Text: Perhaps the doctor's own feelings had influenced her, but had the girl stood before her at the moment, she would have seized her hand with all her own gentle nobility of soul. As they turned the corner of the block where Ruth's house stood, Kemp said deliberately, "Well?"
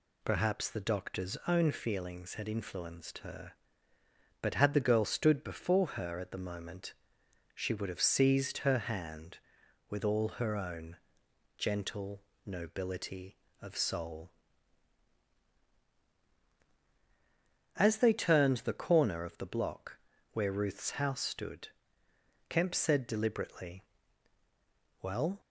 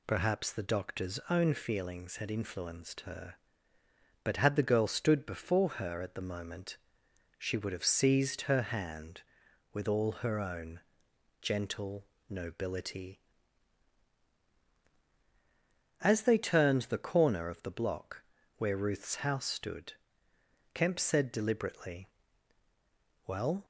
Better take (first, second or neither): first